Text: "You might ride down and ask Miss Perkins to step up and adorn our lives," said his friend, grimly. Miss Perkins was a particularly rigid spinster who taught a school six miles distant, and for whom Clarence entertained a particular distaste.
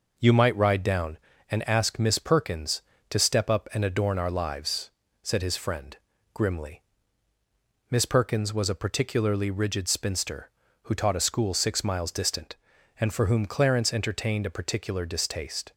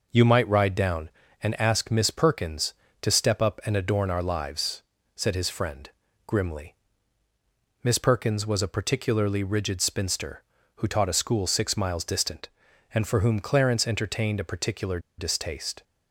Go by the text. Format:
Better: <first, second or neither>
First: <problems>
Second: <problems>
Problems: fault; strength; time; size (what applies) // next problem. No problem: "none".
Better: first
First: none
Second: pauses between "particular" and "distaste"; slight; at 14.9 s; 0.19 s long